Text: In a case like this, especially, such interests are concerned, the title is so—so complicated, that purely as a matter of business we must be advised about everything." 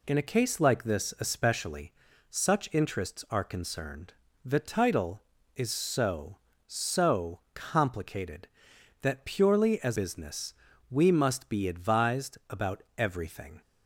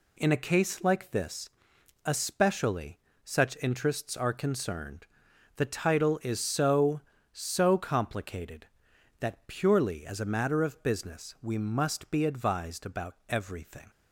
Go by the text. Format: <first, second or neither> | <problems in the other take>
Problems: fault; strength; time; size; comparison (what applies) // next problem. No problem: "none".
second | skips "a matter of"; at 9.9 s // pauses between "business" and "we"; at 10.5 s; 0.38 s long // pauses between "about" and "everything"; slight; at 12.8 s; 0.16 s long